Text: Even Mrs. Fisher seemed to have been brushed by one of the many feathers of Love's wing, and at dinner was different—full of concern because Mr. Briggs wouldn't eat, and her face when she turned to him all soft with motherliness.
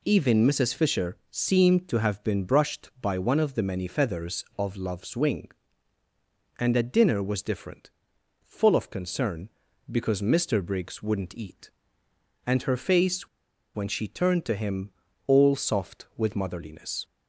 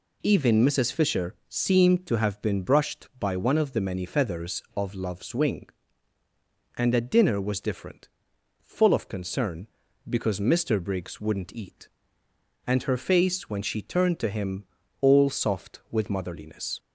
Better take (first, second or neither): second